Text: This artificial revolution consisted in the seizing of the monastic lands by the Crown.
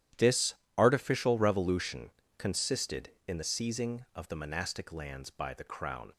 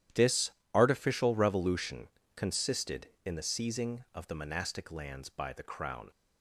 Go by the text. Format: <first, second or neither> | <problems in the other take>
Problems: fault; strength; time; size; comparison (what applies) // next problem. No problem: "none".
neither | starts louder than the rest; strong; the same in both // pauses between "This" and "artificial"; slight; the same in both // pauses between "revolution" and "consisted"; slight; the same in both